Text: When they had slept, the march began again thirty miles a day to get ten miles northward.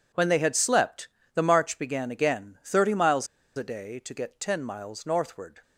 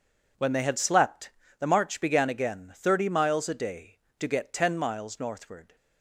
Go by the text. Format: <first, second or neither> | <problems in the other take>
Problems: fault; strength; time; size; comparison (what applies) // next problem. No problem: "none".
second | pauses between "miles" and "a"; slight; at 3.2 s; 0.30 s long